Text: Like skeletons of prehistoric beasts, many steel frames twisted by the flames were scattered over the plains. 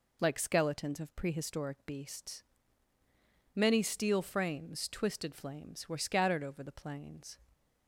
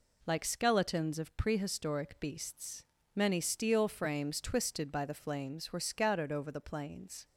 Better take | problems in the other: second | skips "by the"; at 5.3 s

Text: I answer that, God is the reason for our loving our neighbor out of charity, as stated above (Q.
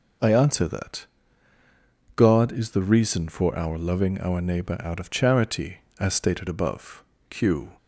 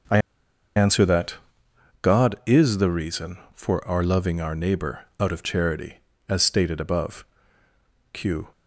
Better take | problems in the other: first | starts louder than the rest; noticeable; until 2.3 s; 6 dB // pauses between "I" and "answer"; noticeable; at 0.1 s; 0.58 s long

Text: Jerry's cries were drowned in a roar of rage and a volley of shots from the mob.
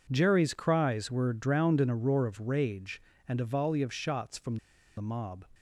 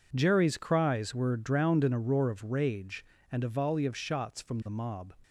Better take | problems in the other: second | pauses between "from" and "the"; at 4.5 s; 0.41 s long

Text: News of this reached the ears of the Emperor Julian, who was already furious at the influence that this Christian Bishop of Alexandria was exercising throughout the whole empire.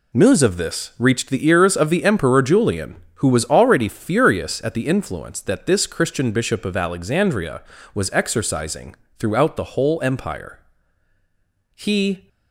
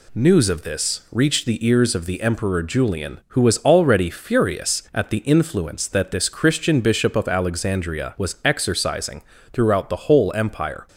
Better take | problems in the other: second | pauses between "exercising" and "throughout"; slight; at 8.9 s; 0.24 s long; slight in the second // goes on to say "He"; from 11.7 s on; 0.54 s long

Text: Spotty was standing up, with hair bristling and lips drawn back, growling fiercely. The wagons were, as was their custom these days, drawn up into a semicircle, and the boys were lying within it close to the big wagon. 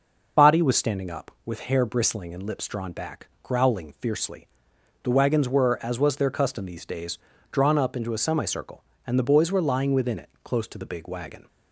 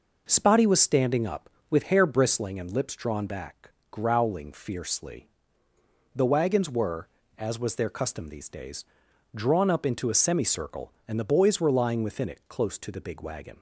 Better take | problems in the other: second | loses the start of "Spotty"; at 0.3 s; 145 ms

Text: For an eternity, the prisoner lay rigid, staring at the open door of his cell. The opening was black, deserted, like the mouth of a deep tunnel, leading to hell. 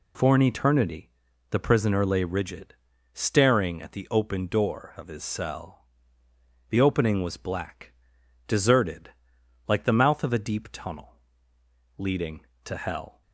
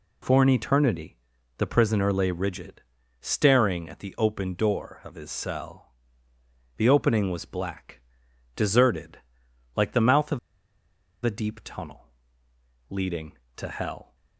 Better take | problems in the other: first | pauses between "of" and "a"; noticeable; at 10.3 s; 0.83 s long

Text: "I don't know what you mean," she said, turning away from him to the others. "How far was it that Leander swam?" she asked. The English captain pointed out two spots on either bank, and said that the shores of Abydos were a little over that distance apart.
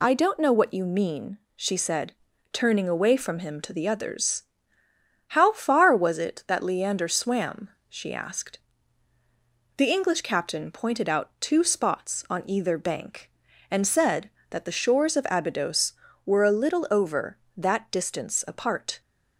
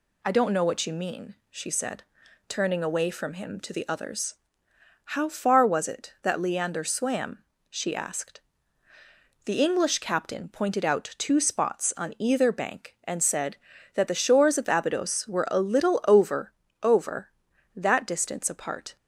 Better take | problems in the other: first | says "over" twice; at 16.8 s

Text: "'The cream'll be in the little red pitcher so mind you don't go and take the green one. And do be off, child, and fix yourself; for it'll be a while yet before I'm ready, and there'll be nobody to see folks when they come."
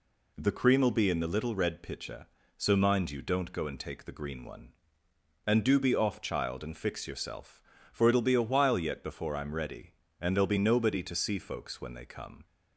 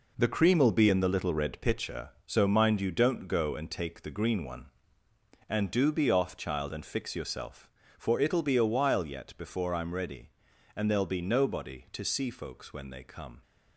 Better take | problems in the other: first | gets quieter; strong; throughout; 9 dB

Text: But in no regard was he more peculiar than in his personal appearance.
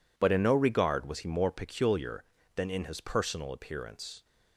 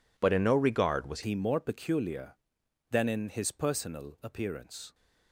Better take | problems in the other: first | changes voice at "he"; from 1.2 s on; 3.7 s long

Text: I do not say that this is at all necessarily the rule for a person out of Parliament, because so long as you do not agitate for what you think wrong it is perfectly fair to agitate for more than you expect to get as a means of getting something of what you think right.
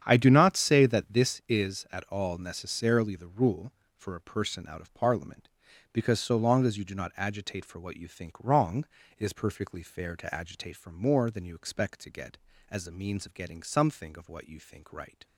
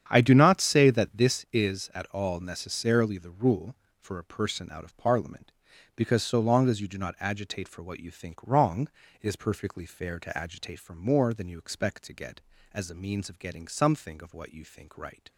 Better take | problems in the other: neither | starts louder than the rest; strong; the same in both // pauses between "wrong" and "it"; slight; the same in both

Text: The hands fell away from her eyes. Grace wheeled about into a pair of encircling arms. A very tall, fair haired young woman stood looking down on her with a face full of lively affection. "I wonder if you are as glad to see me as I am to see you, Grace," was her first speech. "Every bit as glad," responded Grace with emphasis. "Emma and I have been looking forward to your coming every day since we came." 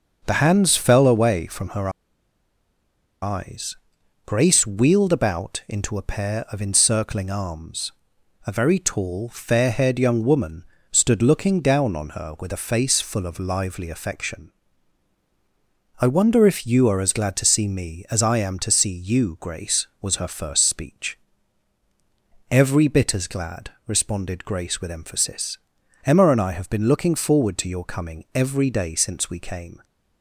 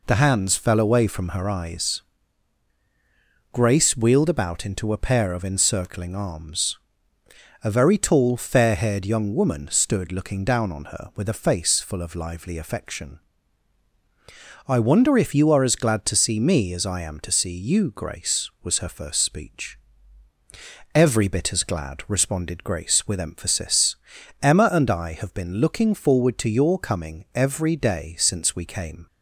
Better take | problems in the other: second | starts louder than the rest; noticeable; until 1.2 s; 6 dB // pauses between "her" and "eyes"; strong; at 1.8 s; 1.3 s long // pauses between "woman" and "stood"; slight; at 10.6 s; 0.26 s long

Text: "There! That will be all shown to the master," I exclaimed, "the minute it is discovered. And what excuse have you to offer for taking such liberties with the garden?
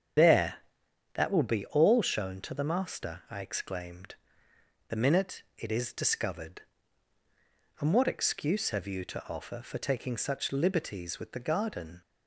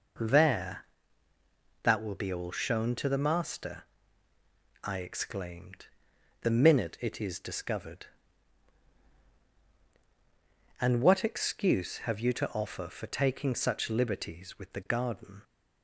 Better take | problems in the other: second | loses the start of "There"; at 0.1 s; 60 ms // starts louder than the rest; strong; until 1.7 s; 7.5 dB

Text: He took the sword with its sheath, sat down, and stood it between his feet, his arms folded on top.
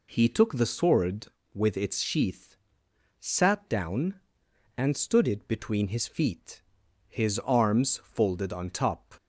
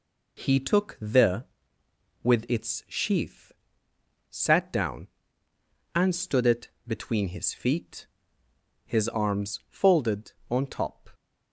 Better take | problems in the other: first | skips "sword"; at 1.8 s // pauses between "it" and "between"; slight; at 6.6 s; 0.18 s long

